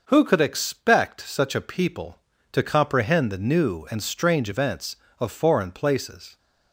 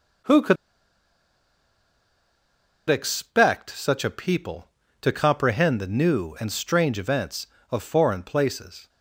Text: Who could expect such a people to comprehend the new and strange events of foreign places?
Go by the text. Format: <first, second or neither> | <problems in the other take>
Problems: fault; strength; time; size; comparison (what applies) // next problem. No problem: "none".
first | pauses between "could" and "expect"; strong; at 0.5 s; 2.3 s long